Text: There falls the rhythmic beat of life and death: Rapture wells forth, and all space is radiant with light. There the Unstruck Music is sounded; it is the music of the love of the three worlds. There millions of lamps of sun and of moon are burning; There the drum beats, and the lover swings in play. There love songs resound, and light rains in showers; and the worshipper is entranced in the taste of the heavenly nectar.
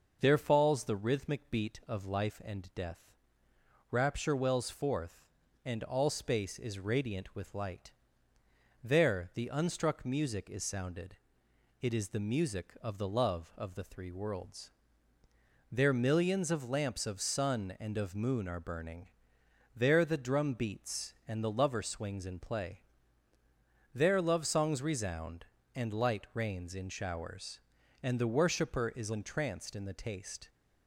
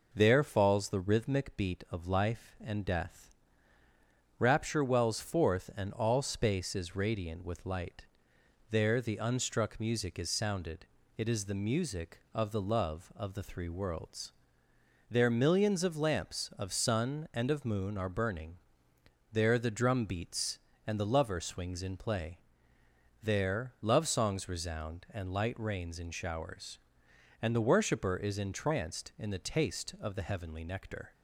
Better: second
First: starts louder than the rest; noticeable; until 1.2 s; 6 dB // stops before "of the heavenly nectar"; at 30.4 s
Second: none

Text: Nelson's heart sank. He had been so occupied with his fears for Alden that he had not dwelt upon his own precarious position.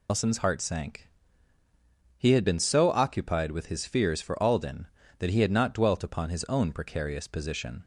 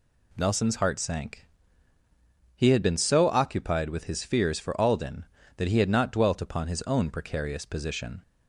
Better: second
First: loses the start of "Nelson's"; at 0.0 s; 155 ms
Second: none

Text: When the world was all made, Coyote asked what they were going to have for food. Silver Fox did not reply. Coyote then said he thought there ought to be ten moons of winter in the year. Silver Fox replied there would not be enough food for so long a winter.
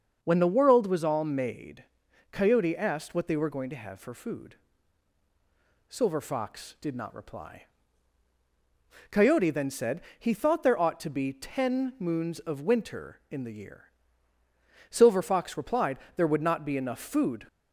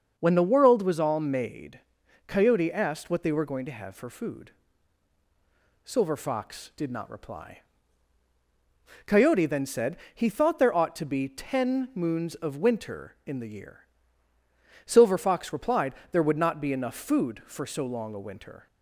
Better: second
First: starts louder than the rest; until 1.2 s; 6.5 dB // pauses between "said" and "he"; slight; at 10.0 s; 0.18 s long // pauses between "replied" and "there"; slight; at 15.9 s; 0.20 s long // stops before "for so long a winter"; at 17.4 s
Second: starts louder than the rest; until 1.1 s; 6.5 dB // pauses between "said" and "he"; slight; at 9.9 s; 0.18 s long // pauses between "replied" and "there"; slight; at 15.9 s; 0.20 s long

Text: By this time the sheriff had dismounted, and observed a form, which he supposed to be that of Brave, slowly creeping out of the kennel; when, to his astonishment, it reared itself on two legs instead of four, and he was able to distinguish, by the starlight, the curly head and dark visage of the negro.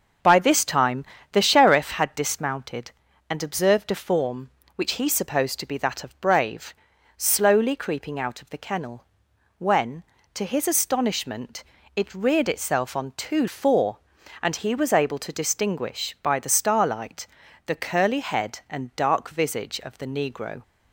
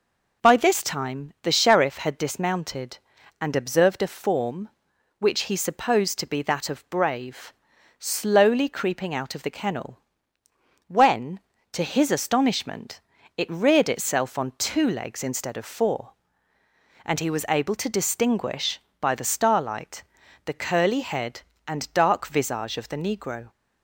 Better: second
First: starts louder than the rest; until 1.5 s; 6.5 dB // pauses between "time" and "the"; slight; at 1.0 s; 0.28 s long // skips "legs instead of"; at 13.4 s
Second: none

